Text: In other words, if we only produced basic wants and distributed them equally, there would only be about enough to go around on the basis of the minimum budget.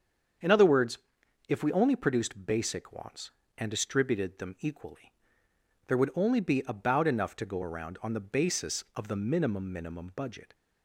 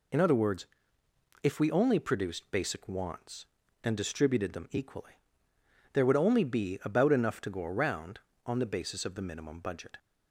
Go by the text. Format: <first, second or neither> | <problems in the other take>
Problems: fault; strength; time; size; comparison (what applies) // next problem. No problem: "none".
second | starts louder than the rest; strong; until 1.9 s; 7.5 dB // says "minimum" twice; at 9.7 s